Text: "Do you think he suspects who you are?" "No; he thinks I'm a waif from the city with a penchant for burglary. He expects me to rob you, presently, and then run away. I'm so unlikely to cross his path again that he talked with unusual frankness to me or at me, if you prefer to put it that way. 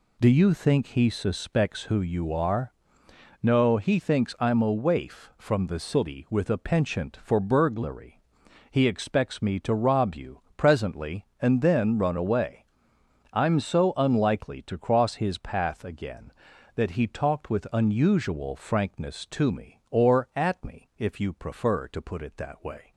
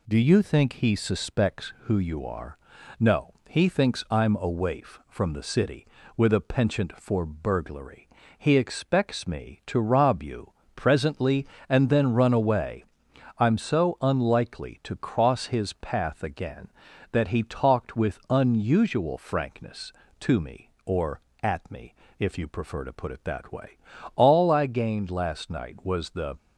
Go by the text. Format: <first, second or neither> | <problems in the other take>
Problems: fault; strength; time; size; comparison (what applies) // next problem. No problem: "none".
first | goes on to say "All I gained last night was the"; strong; from 24.1 s on; 2.2 s long